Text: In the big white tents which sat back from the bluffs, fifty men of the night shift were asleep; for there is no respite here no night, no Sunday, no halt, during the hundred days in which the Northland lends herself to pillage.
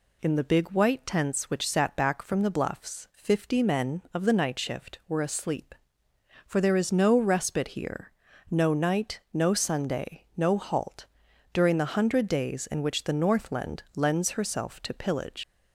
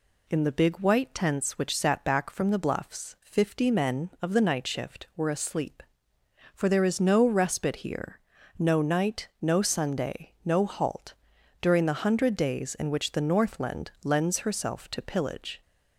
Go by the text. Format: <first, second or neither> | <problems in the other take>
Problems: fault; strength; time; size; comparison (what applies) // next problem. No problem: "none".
second | pauses between "here" and "no"; at 8.1 s; 0.38 s long; also in the second // leaves "pillage" unfinished; at 15.4 s; 95 ms